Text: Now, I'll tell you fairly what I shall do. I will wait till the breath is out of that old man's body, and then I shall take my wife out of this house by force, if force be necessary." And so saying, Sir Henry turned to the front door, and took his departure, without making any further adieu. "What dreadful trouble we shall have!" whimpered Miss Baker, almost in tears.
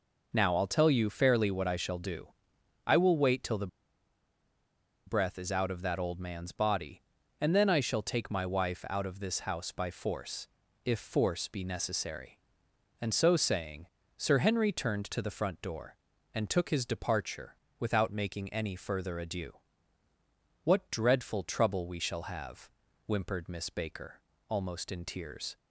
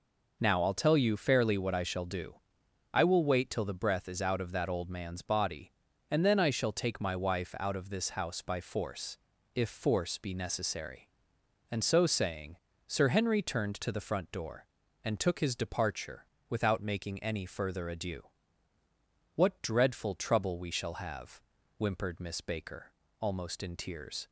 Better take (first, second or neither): second